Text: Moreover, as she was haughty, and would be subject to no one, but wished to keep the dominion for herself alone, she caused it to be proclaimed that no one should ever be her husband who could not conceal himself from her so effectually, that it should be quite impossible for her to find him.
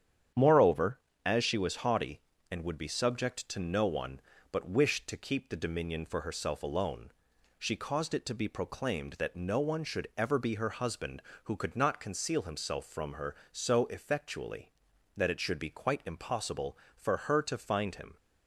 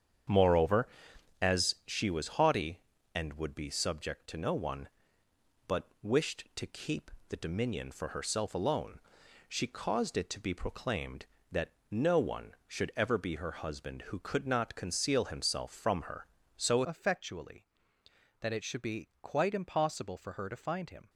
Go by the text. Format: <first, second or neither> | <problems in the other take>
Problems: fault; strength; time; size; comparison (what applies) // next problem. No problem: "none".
first | starts louder than the rest; strong; until 1.9 s; 8 dB; strong in the first // pauses between "keep" and "the"; slight; at 7.1 s; 0.20 s long // pauses between "that" and "no"; slight; at 11.7 s; 0.20 s long // changes voice at "effectually"; from 16.8 s on; 4.2 s long